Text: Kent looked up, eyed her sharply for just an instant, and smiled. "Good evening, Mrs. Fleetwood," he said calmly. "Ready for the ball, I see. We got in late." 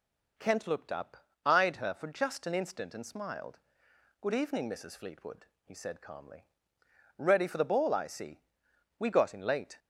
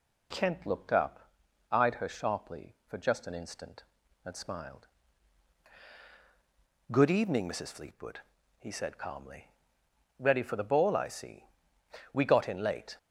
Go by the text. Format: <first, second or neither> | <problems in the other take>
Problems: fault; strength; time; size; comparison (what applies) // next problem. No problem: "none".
second | skips "sharply"; at 1.9 s